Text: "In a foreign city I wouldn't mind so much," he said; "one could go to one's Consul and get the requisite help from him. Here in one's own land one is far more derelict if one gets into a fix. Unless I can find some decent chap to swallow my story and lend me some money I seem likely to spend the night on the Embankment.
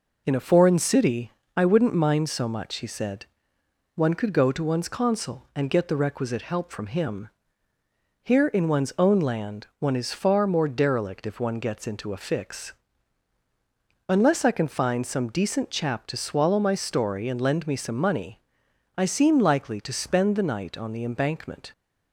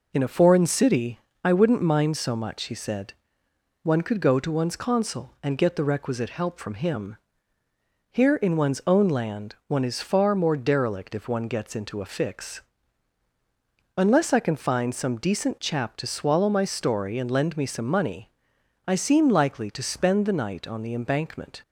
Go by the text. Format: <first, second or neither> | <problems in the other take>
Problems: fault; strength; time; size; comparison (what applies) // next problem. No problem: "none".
neither | pauses between "city" and "I"; slight; the same in both // pauses between "money" and "I"; noticeable; the same in both